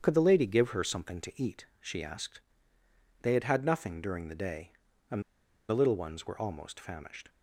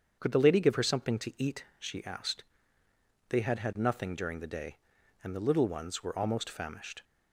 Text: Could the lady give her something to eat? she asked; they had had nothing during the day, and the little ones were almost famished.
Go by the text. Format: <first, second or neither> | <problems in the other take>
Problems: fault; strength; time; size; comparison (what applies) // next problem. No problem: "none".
second | starts louder than the rest; strong; until 1.0 s; 8 dB; strong in the second // pauses between "and" and "the"; noticeable; at 5.2 s; 0.46 s long